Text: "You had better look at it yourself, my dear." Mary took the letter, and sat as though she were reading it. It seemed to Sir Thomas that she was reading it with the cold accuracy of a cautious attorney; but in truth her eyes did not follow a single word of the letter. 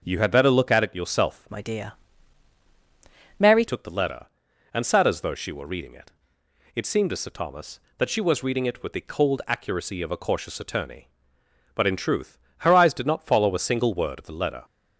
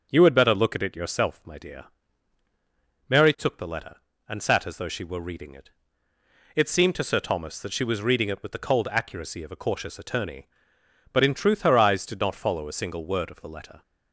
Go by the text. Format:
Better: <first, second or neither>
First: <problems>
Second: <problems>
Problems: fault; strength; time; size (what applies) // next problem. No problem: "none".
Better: second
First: starts louder than the rest; strong; until 1.0 s; 7.5 dB // changes voice from "my" to "Mary"; from 1.5 to 3.6 s; 2.1 s long // pauses between "truth" and "her"; slight; at 12.3 s; 0.22 s long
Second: none